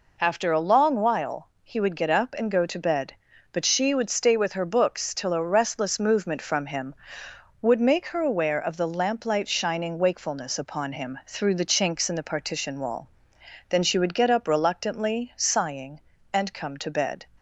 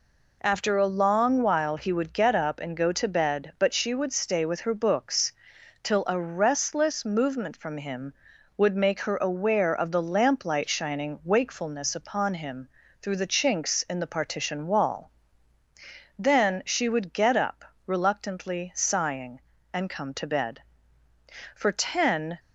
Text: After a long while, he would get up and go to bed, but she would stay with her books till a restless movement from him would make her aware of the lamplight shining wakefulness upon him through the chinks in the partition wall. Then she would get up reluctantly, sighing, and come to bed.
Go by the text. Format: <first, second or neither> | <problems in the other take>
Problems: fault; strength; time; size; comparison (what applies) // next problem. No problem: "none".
first | pauses between "books" and "till"; noticeable; at 5.3 s; 0.50 s long // pauses between "him" and "through"; slight; at 12.6 s; 0.34 s long // pauses between "up" and "reluctantly"; slight; at 17.6 s; 0.20 s long // goes on to say "For ten"; noticeable; from 21.5 s on; 0.82 s long